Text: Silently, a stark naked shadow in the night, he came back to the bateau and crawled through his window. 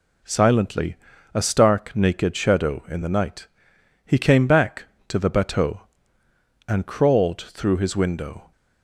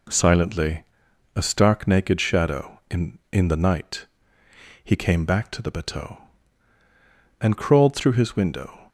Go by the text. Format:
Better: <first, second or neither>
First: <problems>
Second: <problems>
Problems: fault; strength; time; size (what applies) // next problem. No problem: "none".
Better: first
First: none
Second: says "in" twice; at 3.3 s